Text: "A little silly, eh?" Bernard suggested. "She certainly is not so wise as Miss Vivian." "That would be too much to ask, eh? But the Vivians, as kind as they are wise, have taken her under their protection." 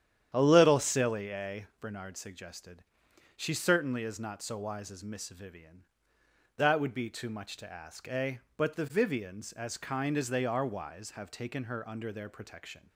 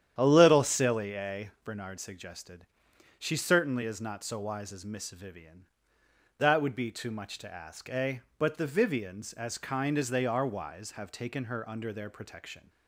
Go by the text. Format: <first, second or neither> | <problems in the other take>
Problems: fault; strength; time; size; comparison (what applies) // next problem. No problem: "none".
neither | starts louder than the rest; strong; the same in both